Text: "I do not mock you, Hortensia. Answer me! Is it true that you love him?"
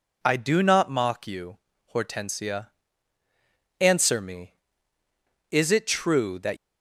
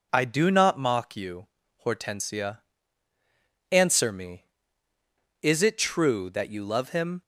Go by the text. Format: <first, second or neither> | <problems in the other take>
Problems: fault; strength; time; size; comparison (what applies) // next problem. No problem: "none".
second | stops before "you love him"; at 6.5 s